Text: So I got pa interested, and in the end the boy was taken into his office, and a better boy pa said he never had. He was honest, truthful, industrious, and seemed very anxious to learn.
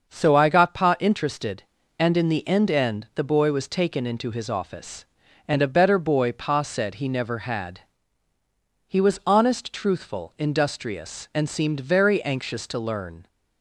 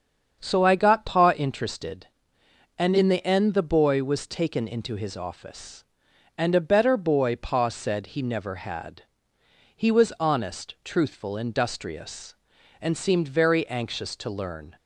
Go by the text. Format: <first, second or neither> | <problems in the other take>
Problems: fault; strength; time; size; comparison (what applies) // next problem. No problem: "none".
second | starts louder than the rest; until 1.1 s; 6.5 dB; strong in the second // says "end" twice; at 2.7 s